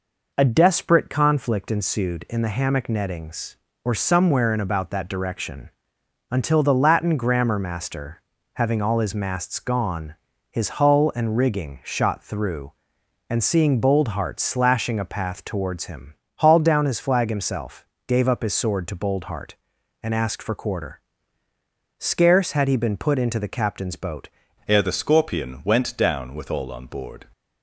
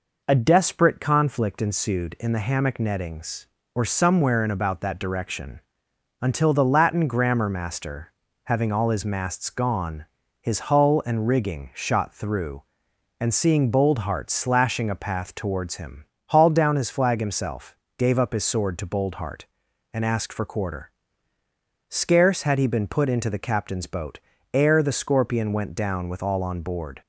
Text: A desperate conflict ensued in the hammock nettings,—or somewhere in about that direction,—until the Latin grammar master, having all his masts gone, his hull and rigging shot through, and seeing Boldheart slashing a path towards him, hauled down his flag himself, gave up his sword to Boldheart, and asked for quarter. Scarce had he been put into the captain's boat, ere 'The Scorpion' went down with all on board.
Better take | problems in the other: second | changes voice at "ere"; from 24.6 s on; 2.6 s long

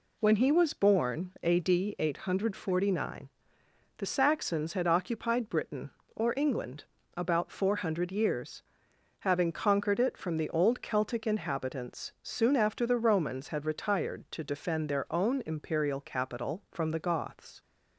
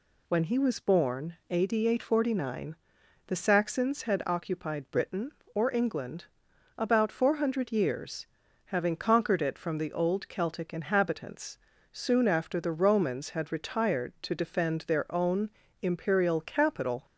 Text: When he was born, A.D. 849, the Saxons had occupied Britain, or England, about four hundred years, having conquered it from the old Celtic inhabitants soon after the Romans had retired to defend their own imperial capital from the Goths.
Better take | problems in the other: first | pauses between "inhabitants" and "soon"; slight; at 11.5 s; 0.34 s long // pauses between "own" and "imperial"; slight; at 15.5 s; 0.32 s long // stops before "from the Goths"; at 17.0 s

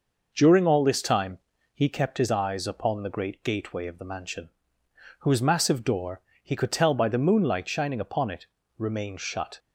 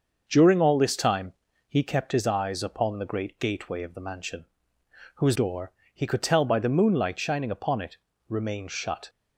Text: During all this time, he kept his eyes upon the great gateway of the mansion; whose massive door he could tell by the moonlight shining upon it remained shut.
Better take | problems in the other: first | starts louder than the rest; until 1.2 s; 6 dB // skips "massive"; at 5.3 s // pauses between "door" and "he"; slight; at 5.7 s; 0.24 s long; slight in the first // pauses between "it" and "remained"; slight; at 7.9 s; 0.32 s long; slight in the first

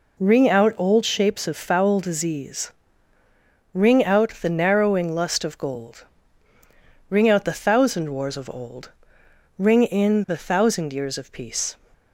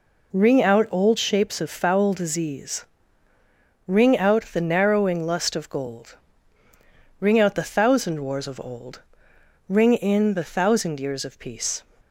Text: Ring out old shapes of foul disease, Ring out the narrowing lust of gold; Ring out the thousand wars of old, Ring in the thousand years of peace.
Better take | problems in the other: neither | none

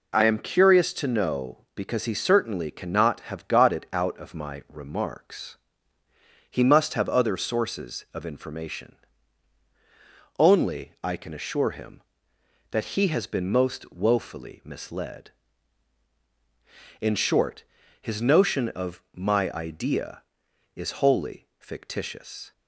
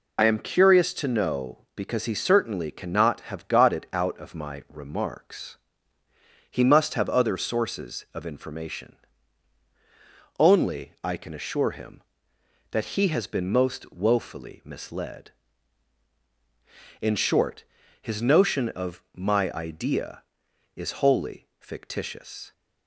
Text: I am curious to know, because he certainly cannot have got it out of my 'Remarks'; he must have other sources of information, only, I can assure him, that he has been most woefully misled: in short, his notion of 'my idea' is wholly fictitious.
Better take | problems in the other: first | loses the start of "I"; at 0.1 s; 55 ms

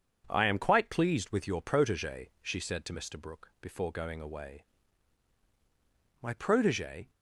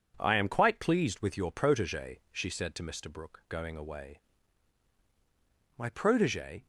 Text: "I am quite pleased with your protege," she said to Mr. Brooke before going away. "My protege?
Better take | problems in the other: first | skips "before"; at 3.4 s

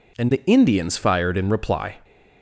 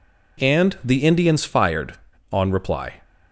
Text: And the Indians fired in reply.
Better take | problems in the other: first | says "on" for "in"; at 2.3 s

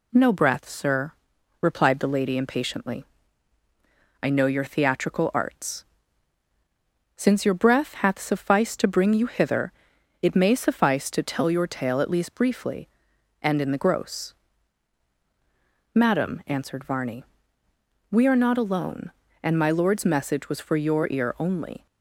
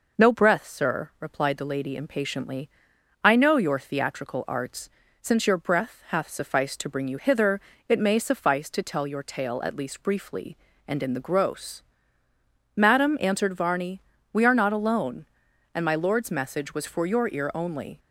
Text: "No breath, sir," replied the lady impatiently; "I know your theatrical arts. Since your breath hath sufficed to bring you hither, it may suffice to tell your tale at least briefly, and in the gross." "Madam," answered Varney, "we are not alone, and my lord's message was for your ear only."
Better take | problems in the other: neither | none

